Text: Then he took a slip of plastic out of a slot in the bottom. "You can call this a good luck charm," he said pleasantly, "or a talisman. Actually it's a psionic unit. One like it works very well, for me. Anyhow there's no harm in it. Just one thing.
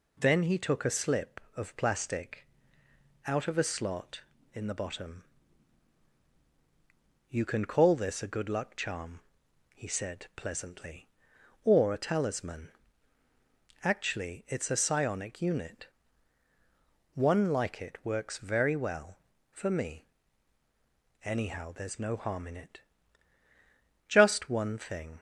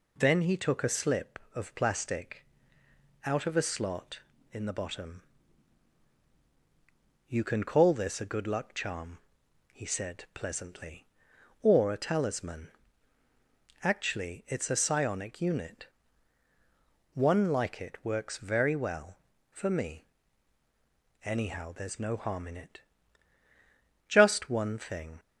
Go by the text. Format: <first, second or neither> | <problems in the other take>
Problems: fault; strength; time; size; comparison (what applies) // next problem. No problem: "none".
neither | pauses between "plastic" and "out"; noticeable; the same in both